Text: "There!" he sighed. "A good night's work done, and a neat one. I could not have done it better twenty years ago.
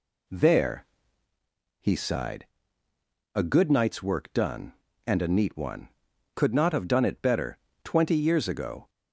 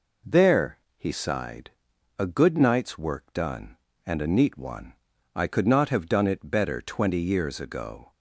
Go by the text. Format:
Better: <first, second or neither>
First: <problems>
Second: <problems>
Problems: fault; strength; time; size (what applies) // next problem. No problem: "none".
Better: second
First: skips "I"; at 6.1 s // pauses between "better" and "twenty"; slight; at 7.5 s; 0.28 s long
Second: none